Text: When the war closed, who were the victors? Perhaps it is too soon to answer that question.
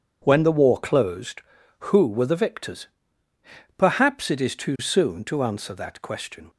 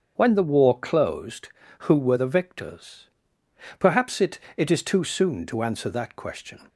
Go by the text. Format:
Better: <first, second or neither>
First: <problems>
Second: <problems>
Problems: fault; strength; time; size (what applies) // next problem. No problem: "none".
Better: first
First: none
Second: starts louder than the rest; until 1.1 s; 7 dB // says "it" twice; at 4.5 s